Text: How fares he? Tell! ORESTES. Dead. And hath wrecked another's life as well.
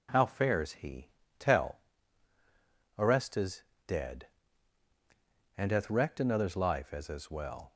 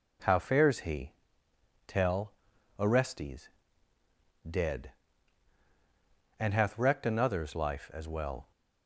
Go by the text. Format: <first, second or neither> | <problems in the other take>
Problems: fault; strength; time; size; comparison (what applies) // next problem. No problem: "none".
second | says "as" twice; at 7.0 s